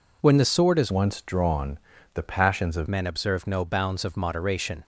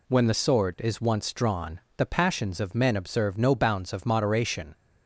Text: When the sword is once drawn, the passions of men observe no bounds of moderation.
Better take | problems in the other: second | changes voice from "once" to "of"; from 0.8 to 2.8 s; 2.0 s long

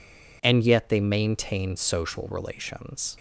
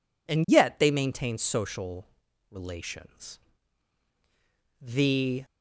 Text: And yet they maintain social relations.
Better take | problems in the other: first | pauses between "social" and "relations"; at 2.0 s; 0.44 s long // goes on to say "The"; noticeable; from 4.8 s on; 0.64 s long

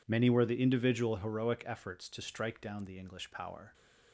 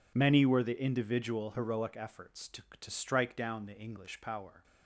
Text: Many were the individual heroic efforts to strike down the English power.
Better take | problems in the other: first | says "to" twice; at 2.7 s

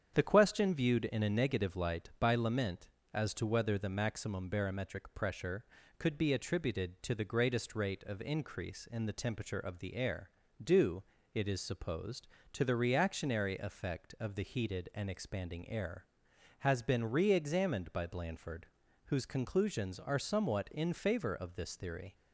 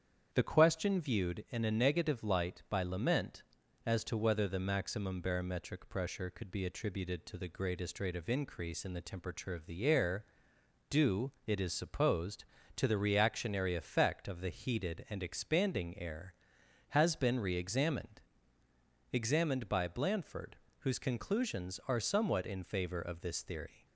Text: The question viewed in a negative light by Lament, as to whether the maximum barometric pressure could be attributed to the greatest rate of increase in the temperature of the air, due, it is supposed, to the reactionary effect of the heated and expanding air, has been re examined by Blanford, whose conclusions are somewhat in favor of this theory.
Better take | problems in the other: first | starts louder than the rest; strong; until 1.3 s; 8 dB; strong in the first // says "examined" twice; at 19.1 s

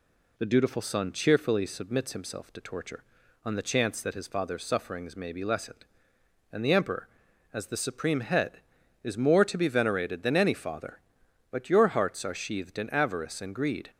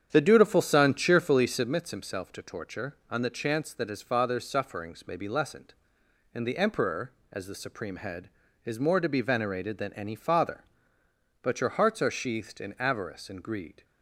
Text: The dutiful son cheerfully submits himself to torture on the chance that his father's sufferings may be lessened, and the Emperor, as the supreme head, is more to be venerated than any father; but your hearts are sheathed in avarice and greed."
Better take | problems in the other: first | starts louder than the rest; strong; until 1.7 s; 8.5 dB

